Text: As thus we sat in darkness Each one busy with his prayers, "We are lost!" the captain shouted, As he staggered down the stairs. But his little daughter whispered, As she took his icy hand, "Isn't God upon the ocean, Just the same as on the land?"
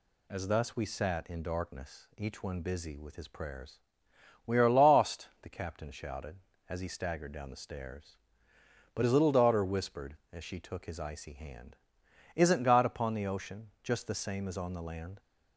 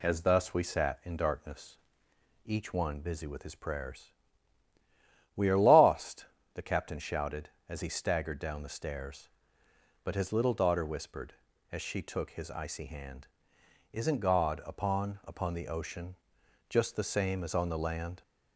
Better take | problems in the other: first | pauses between "darkness" and "Each"; noticeable; at 1.7 s; 0.66 s long // says "upon" twice; at 15.2 s

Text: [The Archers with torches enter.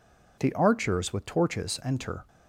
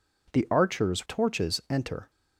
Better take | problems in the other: first | skips "with"; at 1.0 s

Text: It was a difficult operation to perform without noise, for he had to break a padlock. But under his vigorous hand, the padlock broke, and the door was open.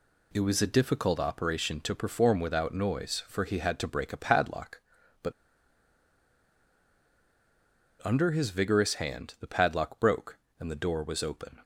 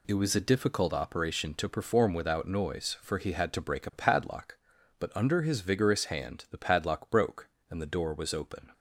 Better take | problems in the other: second | pauses between "But" and "under"; strong; at 5.3 s; 2.7 s long

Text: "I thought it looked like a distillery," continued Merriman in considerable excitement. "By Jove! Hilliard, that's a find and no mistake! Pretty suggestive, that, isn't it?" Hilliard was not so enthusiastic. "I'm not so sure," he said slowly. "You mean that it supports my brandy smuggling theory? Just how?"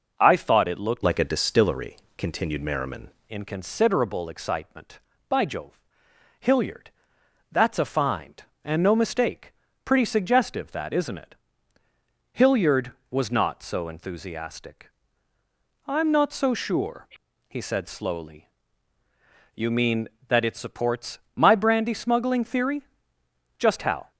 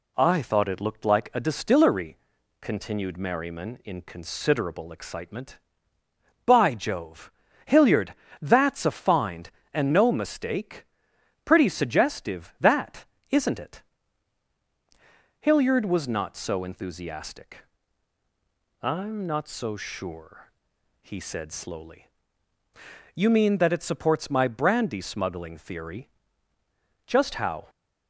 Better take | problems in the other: second | changes voice from "like" to "Merriman"; from 1.0 to 3.0 s; 2.0 s long // pauses between "supports" and "my"; slight; at 21.1 s; 0.16 s long

